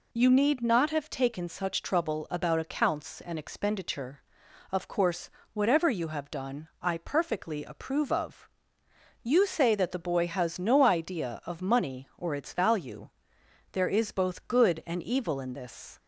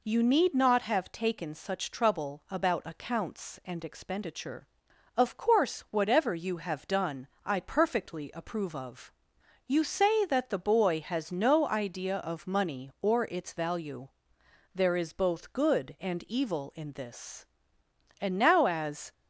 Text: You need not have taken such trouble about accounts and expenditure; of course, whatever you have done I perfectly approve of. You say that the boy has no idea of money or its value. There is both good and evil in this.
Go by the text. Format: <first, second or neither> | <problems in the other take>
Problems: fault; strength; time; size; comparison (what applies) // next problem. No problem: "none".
first | pauses between "done" and "I"; slight; at 7.2 s; 0.16 s long // goes on to say "And now as"; noticeable; from 18.2 s on; 0.92 s long